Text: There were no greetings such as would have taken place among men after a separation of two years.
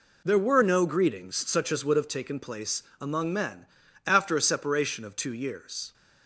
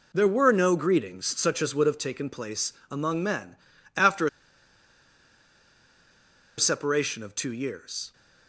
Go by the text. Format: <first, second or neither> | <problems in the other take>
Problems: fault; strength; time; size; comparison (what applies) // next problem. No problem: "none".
first | pauses between "place" and "among"; slight; at 2.7 s; 0.16 s long; slight in the first // pauses between "men" and "after"; at 3.5 s; 0.40 s long; also in the first // pauses between "a" and "separation"; strong; at 4.2 s; 2.3 s long